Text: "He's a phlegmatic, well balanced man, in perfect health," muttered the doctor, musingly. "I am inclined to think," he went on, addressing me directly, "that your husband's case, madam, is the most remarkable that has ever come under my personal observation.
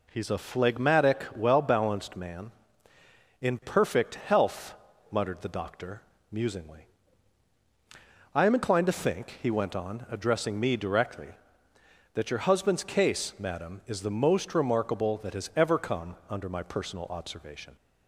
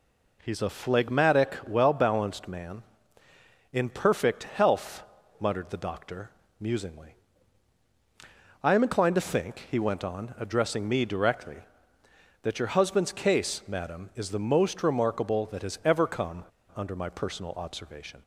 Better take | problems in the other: first | pauses between "come" and "under"; slight; at 16.4 s; 0.31 s long

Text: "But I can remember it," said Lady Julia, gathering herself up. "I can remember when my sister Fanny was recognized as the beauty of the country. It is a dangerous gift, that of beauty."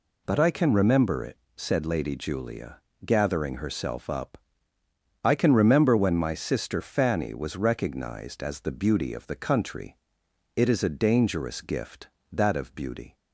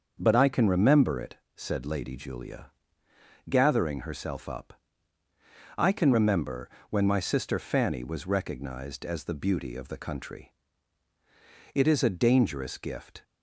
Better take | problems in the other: first | starts louder than the rest; until 1.1 s; 6.5 dB // pauses between "remember" and "when"; slight; at 6.7 s; 0.18 s long // stops before "that of beauty"; at 13.2 s

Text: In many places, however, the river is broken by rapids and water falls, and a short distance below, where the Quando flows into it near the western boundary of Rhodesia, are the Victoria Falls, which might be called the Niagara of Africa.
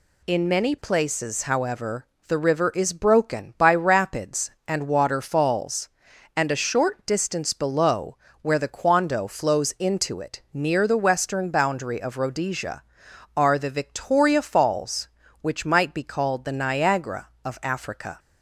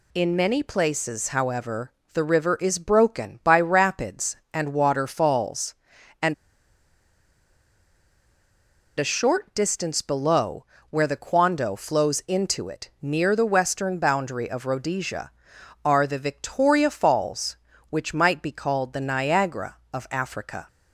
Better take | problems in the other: first | pauses between "and" and "a"; strong; at 6.3 s; 2.6 s long

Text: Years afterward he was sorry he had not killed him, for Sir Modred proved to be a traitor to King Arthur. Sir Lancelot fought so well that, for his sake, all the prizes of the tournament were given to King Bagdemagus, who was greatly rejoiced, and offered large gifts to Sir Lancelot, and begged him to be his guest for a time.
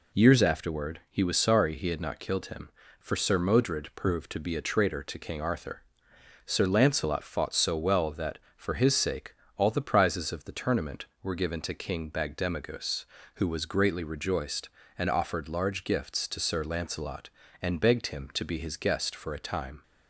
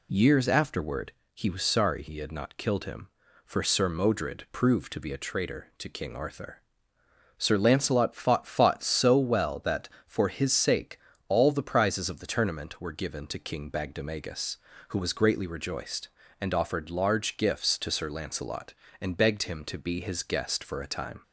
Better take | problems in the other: first | pauses between "afterward" and "he"; slight; at 1.1 s; 0.20 s long // says "fought" twice; at 8.4 s

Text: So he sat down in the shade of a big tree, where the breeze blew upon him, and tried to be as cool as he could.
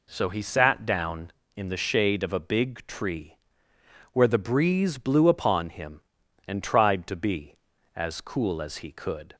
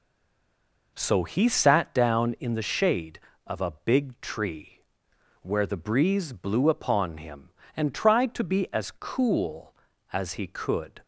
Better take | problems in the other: first | stays silent before the first word; slight; until 0.9 s; 0.9 s long

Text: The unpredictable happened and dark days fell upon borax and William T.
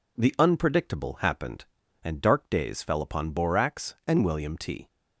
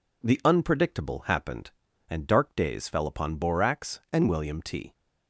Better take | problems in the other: neither | none

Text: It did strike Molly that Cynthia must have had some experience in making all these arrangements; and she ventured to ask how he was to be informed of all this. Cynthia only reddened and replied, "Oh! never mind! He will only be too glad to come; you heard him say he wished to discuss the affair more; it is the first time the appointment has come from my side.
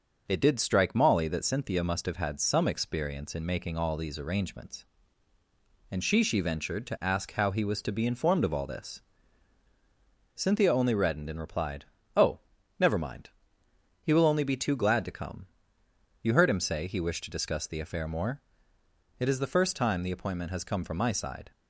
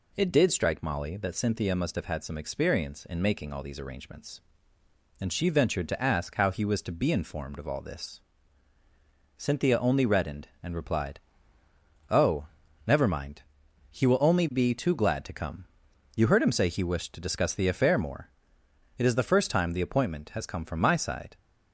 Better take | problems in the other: second | says "she" twice; at 6.2 s

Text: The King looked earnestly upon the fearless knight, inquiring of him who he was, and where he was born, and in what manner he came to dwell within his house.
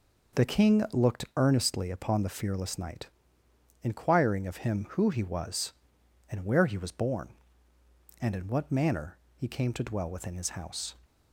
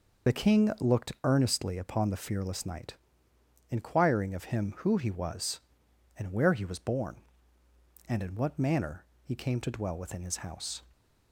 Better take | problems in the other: first | loses the start of "The"; at 0.2 s; 50 ms // pauses between "manner" and "he"; slight; at 9.0 s; 0.20 s long; slight in the first

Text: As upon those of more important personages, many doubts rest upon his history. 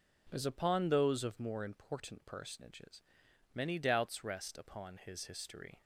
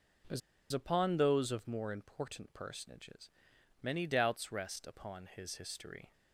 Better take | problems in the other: first | pauses between "As" and "upon"; slight; at 0.4 s; 0.31 s long

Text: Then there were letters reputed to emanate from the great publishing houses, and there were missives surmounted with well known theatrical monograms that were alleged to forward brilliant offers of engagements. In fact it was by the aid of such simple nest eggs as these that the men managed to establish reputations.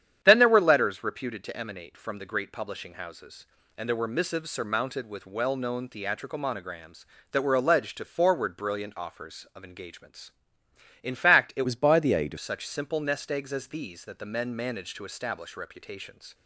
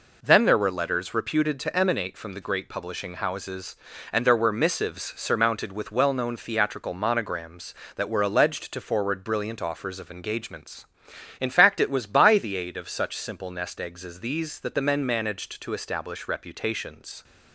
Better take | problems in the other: second | starts louder than the rest; strong; until 1.2 s; 9.5 dB // changes voice from "was" to "of"; from 11.6 to 12.3 s; 0.7 s long

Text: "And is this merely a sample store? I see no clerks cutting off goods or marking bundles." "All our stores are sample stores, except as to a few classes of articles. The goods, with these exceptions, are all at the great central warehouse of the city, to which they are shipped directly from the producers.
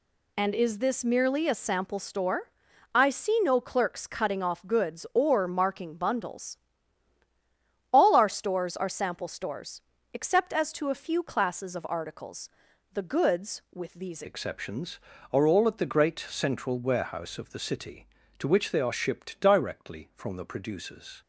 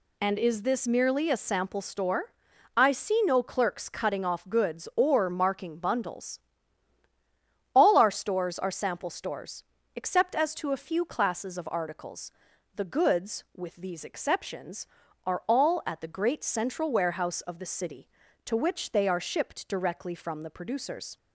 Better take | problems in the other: second | changes voice at "exceptions"; from 14.2 s on; 7.0 s long

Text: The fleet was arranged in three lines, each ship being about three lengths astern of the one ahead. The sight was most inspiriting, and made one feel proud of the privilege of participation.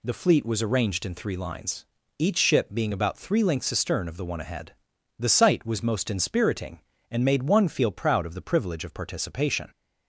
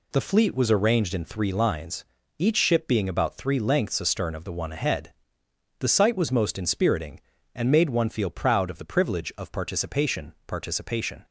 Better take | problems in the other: first | says "participation" twice; at 10.4 s

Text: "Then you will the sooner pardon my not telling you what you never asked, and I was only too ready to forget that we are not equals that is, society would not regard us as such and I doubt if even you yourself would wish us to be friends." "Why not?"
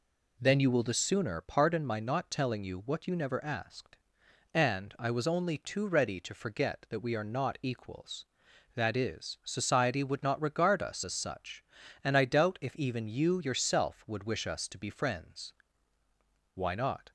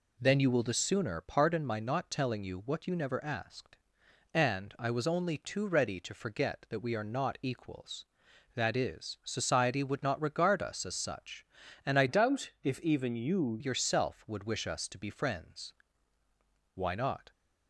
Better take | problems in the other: first | changes voice from "doubt" to "you"; from 12.0 to 13.5 s; 1.5 s long

